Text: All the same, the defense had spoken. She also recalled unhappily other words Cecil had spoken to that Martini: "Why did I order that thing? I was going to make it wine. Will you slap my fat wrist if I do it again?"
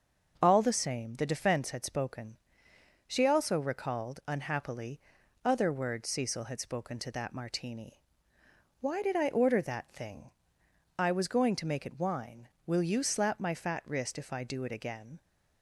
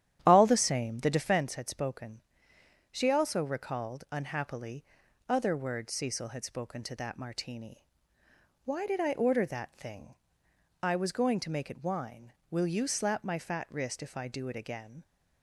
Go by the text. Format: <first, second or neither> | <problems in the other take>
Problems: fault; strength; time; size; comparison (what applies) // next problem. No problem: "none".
first | starts louder than the rest; strong; until 1.4 s; 10.5 dB // pauses between "unhappily" and "other"; at 4.8 s; 0.44 s long; also in the first